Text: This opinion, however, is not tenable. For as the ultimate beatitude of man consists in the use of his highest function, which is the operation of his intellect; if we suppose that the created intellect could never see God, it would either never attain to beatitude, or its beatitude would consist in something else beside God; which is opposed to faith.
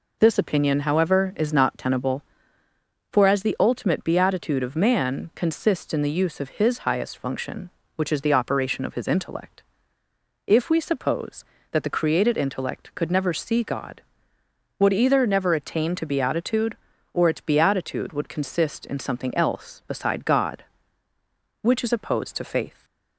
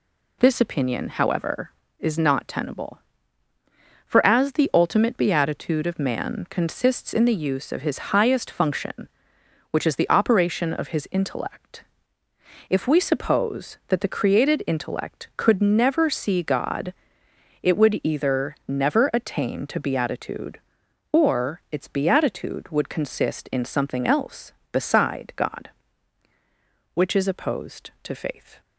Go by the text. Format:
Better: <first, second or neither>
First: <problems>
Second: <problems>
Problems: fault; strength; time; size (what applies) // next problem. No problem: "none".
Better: second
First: skips "it"; at 14.4 s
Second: none